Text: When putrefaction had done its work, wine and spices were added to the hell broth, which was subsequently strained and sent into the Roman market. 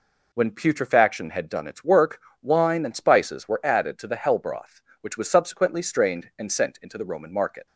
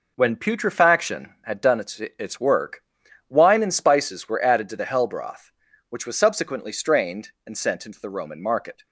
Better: first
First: none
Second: says "its" twice; at 1.9 s

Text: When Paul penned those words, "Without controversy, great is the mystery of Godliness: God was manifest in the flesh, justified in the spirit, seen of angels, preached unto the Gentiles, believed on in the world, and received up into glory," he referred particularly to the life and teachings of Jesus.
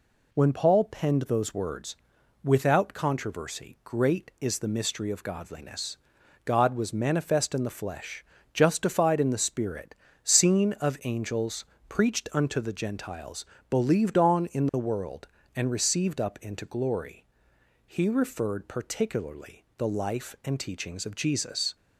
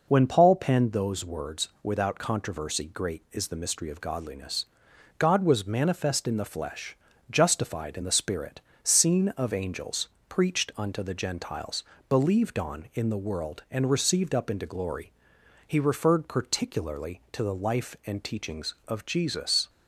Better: second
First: skips "to"; at 19.7 s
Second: none

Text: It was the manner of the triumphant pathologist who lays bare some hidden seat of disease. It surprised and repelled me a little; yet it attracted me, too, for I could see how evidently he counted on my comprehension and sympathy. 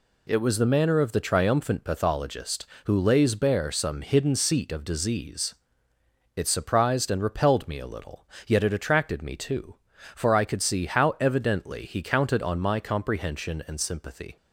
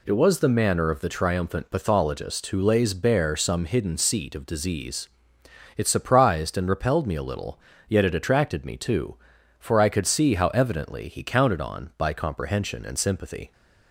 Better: first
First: none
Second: says "by" for "my"; at 11.9 s

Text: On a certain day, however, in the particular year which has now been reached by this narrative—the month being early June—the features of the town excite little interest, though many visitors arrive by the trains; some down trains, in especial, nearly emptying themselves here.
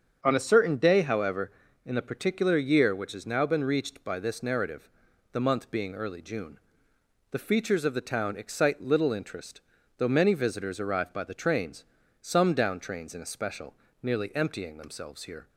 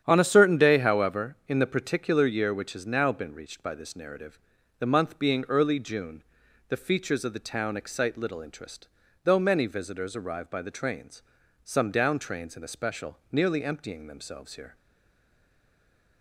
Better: first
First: starts louder than the rest; strong; until 1.2 s; 7 dB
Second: starts louder than the rest; strong; until 1.0 s; 9.5 dB // stays silent after the last word; noticeable; from 14.7 s on; 1.5 s long

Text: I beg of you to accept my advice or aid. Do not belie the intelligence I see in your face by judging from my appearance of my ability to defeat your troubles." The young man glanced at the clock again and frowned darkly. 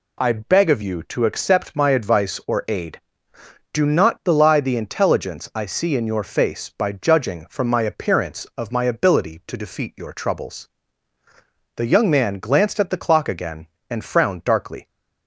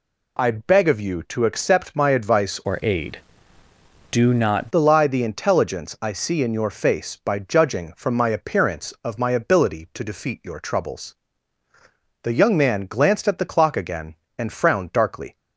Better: first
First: none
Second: changes voice from "or" to "not"; from 2.6 to 4.7 s; 2.1 s long

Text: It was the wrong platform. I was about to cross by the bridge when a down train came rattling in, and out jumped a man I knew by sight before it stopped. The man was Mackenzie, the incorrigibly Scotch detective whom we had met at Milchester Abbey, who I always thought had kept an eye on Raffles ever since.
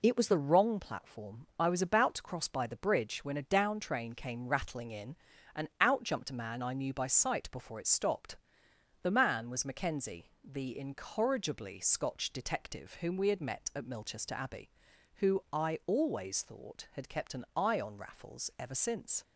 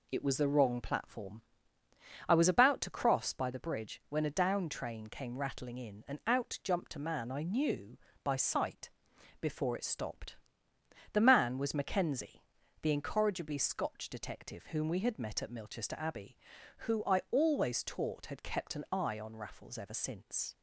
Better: first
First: none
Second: pauses between "sight" and "before"; noticeable; at 8.9 s; 0.50 s long // says "taught" for "thought"; at 17.8 s

